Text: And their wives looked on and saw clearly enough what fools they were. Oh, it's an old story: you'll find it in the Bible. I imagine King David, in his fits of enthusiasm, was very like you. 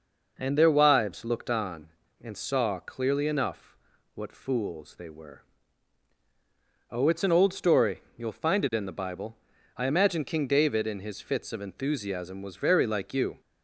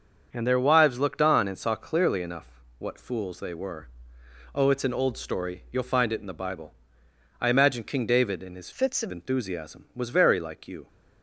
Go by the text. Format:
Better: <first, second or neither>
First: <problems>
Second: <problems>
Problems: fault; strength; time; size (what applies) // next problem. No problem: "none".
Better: first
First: pauses between "enough" and "what"; at 3.7 s; 0.38 s long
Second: starts louder than the rest; until 1.3 s; 6.5 dB // pauses between "enough" and "what"; slight; at 2.4 s; 0.32 s long // changes voice from "fits" to "of"; from 8.7 to 9.1 s; 0.4 s long